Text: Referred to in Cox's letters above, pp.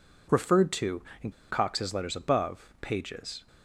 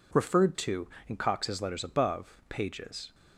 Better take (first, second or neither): second